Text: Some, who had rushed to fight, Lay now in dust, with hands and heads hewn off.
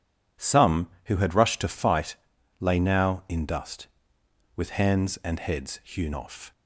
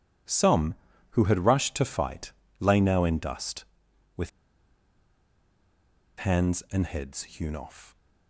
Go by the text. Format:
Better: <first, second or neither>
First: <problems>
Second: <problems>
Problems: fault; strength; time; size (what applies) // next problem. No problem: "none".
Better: first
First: none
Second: pauses between "with" and "hands"; strong; at 4.2 s; 1.8 s long